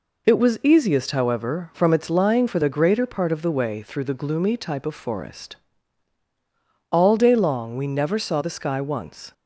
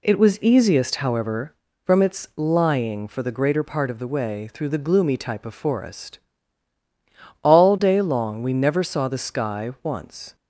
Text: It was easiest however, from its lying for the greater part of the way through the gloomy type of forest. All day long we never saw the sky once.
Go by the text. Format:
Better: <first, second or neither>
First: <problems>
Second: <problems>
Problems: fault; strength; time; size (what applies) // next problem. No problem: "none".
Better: neither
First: none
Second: none